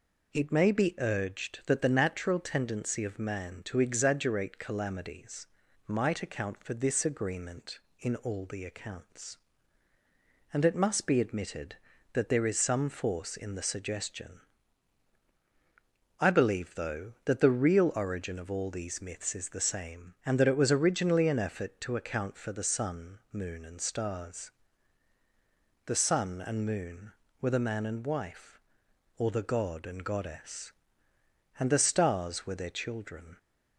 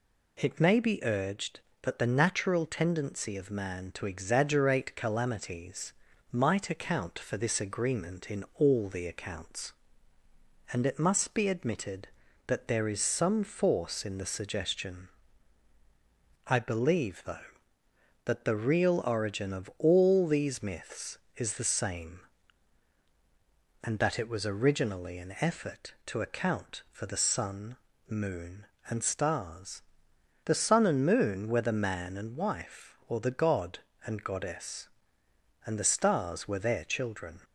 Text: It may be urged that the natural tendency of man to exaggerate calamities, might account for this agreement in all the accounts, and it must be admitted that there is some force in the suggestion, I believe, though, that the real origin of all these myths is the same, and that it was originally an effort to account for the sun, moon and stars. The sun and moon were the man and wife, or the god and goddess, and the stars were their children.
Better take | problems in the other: neither | none

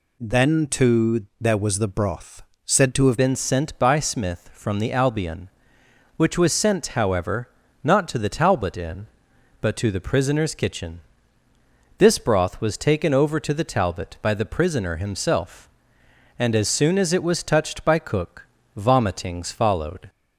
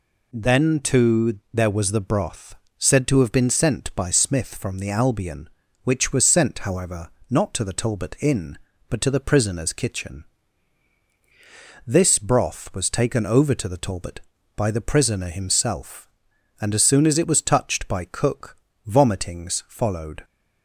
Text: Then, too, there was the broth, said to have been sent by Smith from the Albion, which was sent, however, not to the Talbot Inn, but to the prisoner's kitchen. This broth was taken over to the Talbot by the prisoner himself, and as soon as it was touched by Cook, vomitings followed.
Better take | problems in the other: second | changes voice at "been"; from 3.1 s on; 16.9 s long

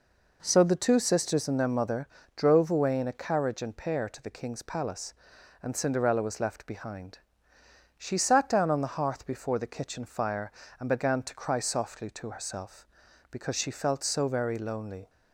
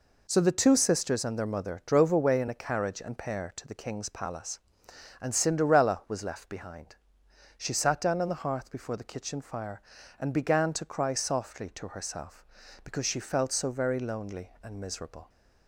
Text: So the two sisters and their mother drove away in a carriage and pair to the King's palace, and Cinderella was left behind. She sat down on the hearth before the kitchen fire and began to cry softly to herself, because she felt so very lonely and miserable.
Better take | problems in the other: second | pauses between "mother" and "drove"; slight; at 2.0 s; 0.28 s long // stops before "and miserable"; at 15.0 s

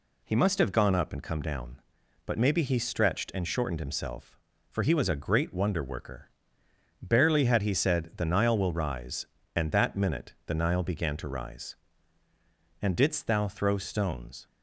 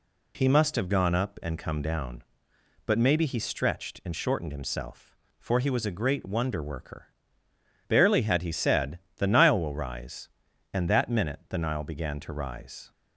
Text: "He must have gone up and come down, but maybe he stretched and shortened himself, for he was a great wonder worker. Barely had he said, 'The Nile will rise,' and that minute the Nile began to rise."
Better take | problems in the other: second | goes on to say "And didst thou throw stones"; from 12.7 s on; 1.6 s long

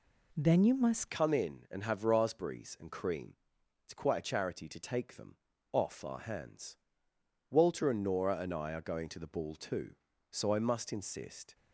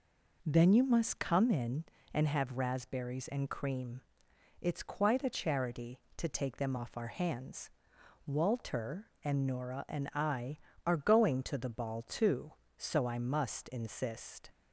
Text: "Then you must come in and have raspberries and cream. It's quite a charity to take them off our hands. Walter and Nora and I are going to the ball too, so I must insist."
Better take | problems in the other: second | changes voice at "come"; from 1.1 s on; 10.4 s long // pauses between "them" and "off"; slight; at 5.3 s; 0.36 s long

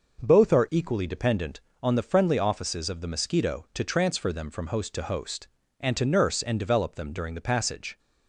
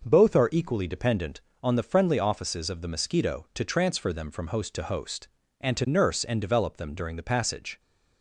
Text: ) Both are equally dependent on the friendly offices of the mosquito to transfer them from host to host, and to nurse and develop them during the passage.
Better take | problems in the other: neither | none

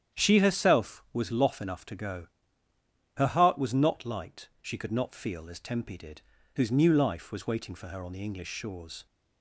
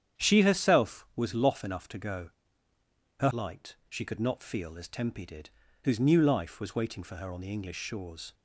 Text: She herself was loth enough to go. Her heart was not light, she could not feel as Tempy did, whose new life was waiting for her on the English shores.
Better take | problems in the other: first | starts louder than the rest; strong; until 1.2 s; 9 dB; strong in the first // skips "heart was not"; at 3.3 s

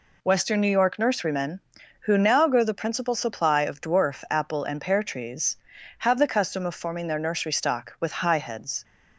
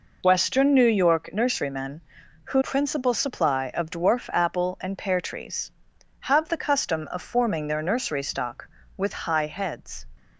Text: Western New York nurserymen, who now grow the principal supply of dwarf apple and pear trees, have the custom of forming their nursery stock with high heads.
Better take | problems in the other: first | skips "now grow the"; at 2.6 s

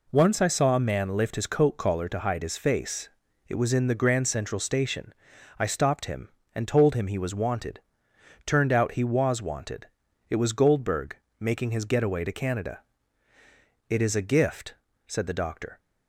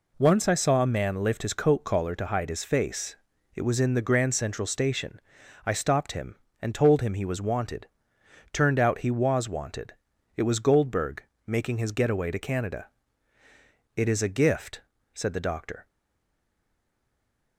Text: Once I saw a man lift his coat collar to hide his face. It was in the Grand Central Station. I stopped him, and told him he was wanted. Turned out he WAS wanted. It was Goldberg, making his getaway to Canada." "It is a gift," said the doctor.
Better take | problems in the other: first | stays silent after the last word; noticeable; from 15.8 s on; 1.7 s long

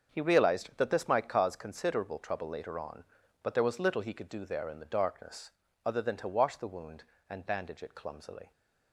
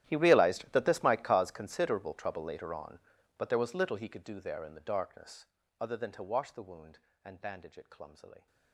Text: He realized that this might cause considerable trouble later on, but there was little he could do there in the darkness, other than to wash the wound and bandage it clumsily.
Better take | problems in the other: first | gets quieter; strong; throughout; 21 dB // starts louder than the rest; strong; until 1.0 s; 12 dB; also in the first

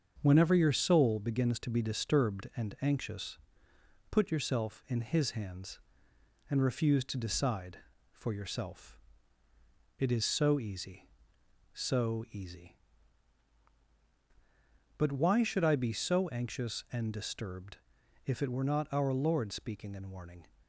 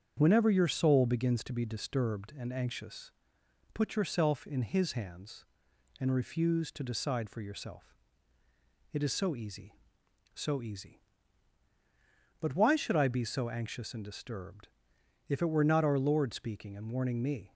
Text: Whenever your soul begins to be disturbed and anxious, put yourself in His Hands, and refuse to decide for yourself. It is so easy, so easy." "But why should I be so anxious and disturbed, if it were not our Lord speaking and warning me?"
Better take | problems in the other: second | starts louder than the rest; until 1.2 s; 7 dB; strong in the second // stops before "me"; at 20.6 s

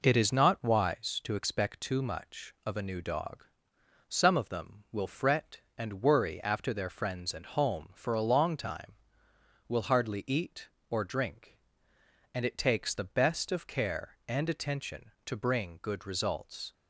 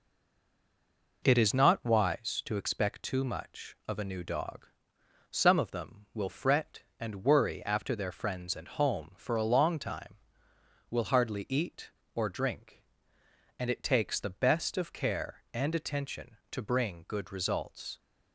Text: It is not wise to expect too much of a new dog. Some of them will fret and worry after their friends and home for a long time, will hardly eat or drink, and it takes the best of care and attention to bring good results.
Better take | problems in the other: first | stays silent before the first word; noticeable; until 1.2 s; 1.2 s long

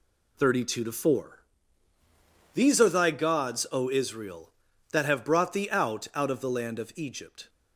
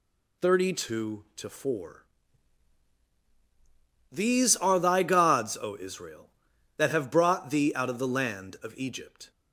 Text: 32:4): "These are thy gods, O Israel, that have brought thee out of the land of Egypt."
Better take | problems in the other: second | says "out" twice; at 6.1 s

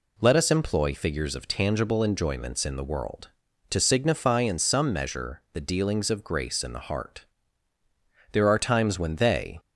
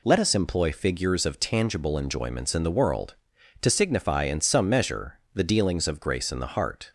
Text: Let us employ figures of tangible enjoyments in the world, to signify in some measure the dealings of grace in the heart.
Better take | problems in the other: second | goes on to say "There are times when they"; noticeable; from 8.3 s on; 1.2 s long

